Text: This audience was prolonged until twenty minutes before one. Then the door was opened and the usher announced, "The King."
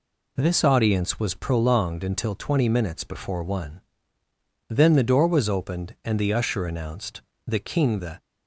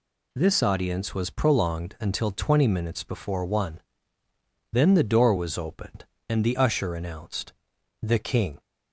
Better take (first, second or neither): second